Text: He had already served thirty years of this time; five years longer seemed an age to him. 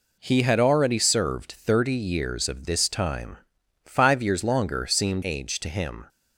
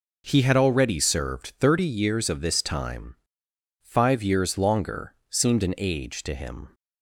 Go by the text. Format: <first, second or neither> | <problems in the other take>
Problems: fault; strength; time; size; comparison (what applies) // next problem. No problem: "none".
second | skips "an"; at 5.2 s